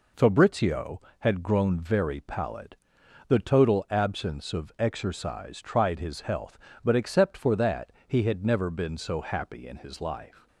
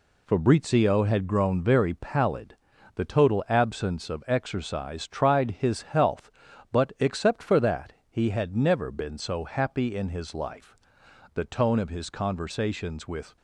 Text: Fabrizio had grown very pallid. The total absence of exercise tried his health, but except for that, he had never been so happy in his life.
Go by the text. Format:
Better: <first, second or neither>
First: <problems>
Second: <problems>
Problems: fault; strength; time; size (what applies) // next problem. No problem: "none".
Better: first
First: none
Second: goes on to say "The tone of his conversations with"; strong; from 11.3 s on; 2.0 s long